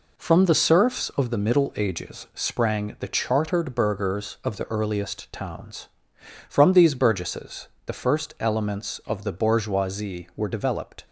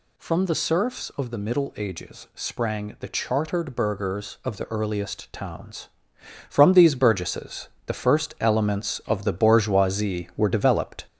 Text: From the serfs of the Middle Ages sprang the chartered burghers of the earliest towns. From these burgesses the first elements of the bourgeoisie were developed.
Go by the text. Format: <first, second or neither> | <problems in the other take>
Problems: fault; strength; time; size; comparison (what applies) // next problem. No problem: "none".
first | gets louder; noticeable; throughout; 4.5 dB // pauses between "burgesses" and "the"; slight; at 7.6 s; 0.18 s long; slight in the first